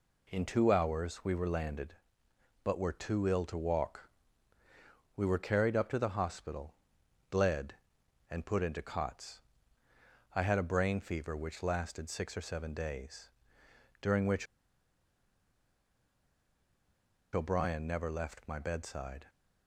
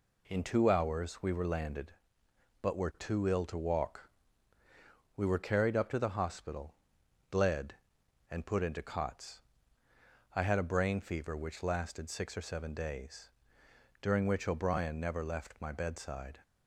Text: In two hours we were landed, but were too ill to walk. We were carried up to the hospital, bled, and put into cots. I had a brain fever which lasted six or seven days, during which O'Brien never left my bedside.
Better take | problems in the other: second | pauses between "which" and "O'Brien"; strong; at 14.4 s; 2.8 s long

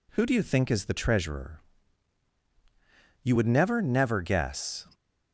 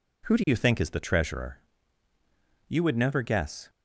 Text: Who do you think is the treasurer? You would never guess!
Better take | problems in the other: second | says "never" twice; at 3.8 s

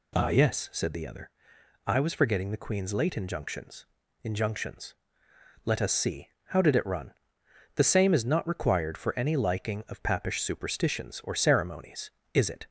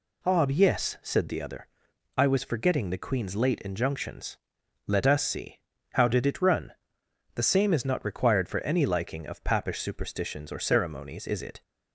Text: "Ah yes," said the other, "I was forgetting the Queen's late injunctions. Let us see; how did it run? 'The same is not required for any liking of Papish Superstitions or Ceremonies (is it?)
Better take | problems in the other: second | says "injunctions" twice; at 4.2 s

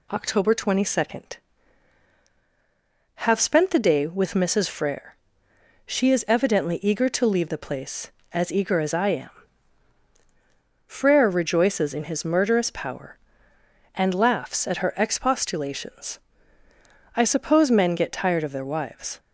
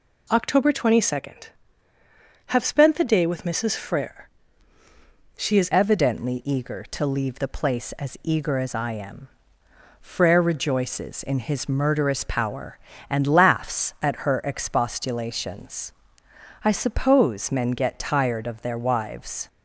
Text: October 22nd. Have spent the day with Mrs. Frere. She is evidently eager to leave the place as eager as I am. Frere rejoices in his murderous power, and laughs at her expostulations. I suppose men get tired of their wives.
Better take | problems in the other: first | changes voice at "evidently"; from 5.7 s on; 13.7 s long

